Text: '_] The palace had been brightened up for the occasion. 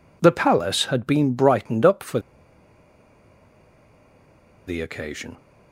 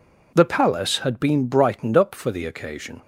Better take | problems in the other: second | pauses between "for" and "the"; strong; at 2.1 s; 2.4 s long

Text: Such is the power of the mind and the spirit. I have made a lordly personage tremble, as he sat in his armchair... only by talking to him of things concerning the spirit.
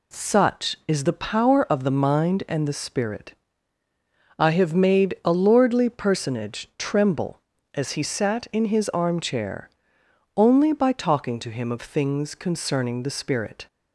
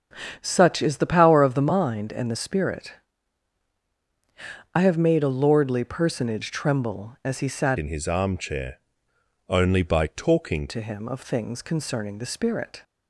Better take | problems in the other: first | starts louder than the rest; strong; until 1.4 s; 8 dB // changes voice from "in" to "talking"; from 7.7 to 10.6 s; 2.9 s long

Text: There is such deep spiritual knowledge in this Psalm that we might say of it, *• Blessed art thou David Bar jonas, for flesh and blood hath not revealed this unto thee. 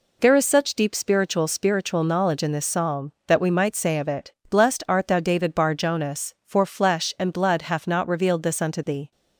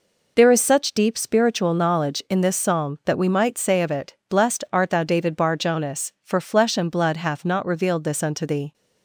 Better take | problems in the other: second | says "spiritual" twice; at 1.4 s

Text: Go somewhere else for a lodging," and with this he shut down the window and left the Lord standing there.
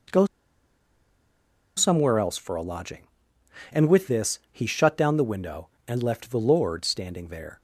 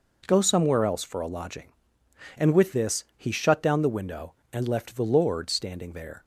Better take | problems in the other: second | pauses between "Go" and "somewhere"; strong; at 0.2 s; 1.5 s long

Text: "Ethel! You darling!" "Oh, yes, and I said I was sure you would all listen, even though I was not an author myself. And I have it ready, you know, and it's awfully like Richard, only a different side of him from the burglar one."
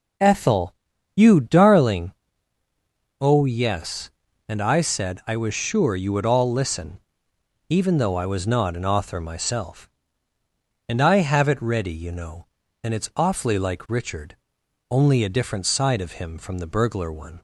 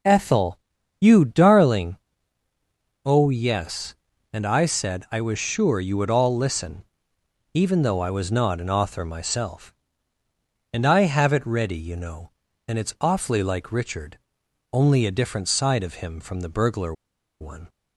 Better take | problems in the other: first | pauses between "burglar" and "one"; at 16.9 s; 0.45 s long

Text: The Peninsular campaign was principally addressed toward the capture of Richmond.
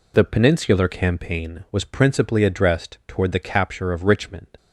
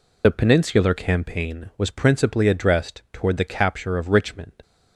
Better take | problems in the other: first | loses the start of "The"; at 0.2 s; 35 ms

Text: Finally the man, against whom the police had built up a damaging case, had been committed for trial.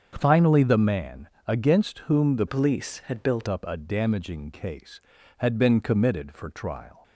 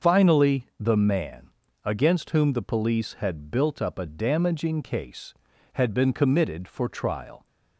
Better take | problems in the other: second | starts louder than the rest; until 1.1 s; 7 dB; also in the second // changes voice from "police" to "built"; from 2.4 to 3.4 s; 1.0 s long

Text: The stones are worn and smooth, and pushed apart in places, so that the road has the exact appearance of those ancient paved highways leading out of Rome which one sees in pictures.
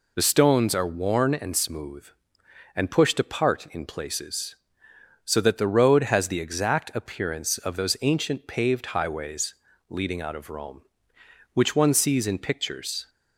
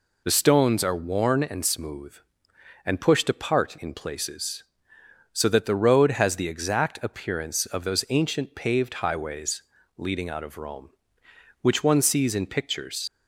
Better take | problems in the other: first | pauses between "highways" and "leading"; slight; at 9.6 s; 0.36 s long; slight in the first // leaves "pictures" unfinished; at 13.0 s; 95 ms

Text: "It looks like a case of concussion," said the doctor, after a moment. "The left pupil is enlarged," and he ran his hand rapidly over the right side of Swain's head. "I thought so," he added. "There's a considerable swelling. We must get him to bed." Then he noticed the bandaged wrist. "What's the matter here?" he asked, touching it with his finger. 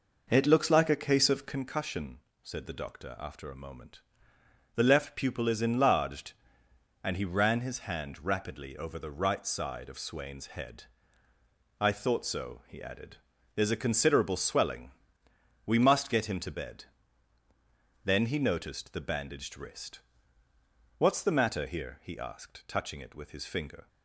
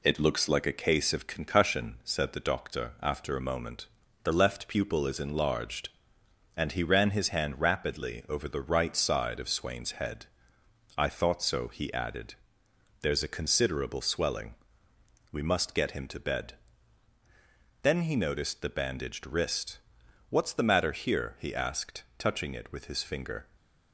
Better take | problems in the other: second | starts louder than the rest; noticeable; until 1.7 s; 5 dB

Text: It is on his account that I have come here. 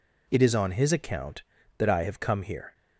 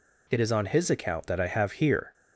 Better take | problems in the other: first | skips "come"; at 1.7 s

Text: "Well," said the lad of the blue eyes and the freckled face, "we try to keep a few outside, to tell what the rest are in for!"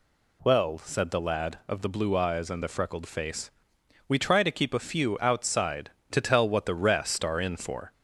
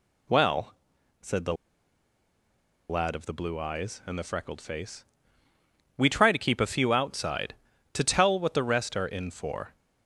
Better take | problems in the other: first | pauses between "the" and "lad"; strong; at 1.5 s; 1.3 s long

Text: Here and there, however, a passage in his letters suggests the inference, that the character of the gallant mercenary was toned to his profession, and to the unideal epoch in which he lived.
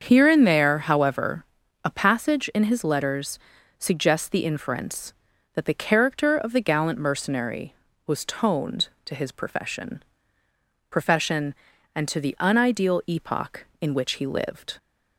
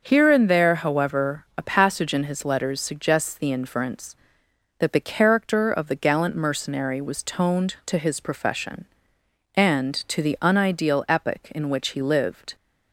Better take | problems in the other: second | starts louder than the rest; until 1.0 s; 6.5 dB; also in the second // pauses between "letters" and "suggests"; at 3.3 s; 0.40 s long // says "profession" twice; at 10.9 s

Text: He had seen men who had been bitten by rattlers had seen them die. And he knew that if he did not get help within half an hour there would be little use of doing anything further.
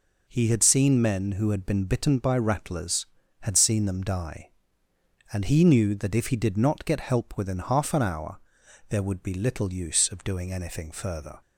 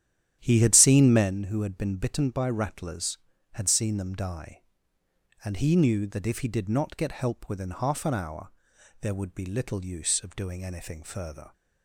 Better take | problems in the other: first | starts louder than the rest; strong; until 1.4 s; 10.5 dB // pauses between "hour" and "there"; noticeable; at 8.4 s; 0.52 s long; noticeable in the first

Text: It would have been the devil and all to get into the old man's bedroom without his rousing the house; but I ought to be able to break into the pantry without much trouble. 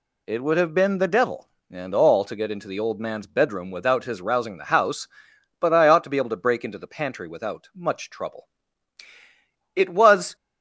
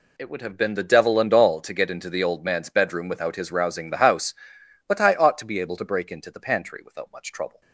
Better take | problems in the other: second | goes on to say "It was"; from 9.7 s on; 0.60 s long

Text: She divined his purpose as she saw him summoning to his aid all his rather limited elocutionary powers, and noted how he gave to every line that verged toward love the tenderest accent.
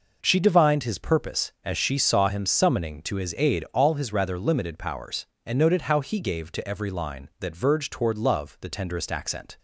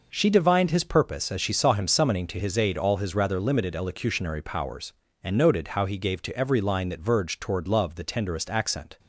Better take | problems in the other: second | skips "elocutionary"; at 4.7 s

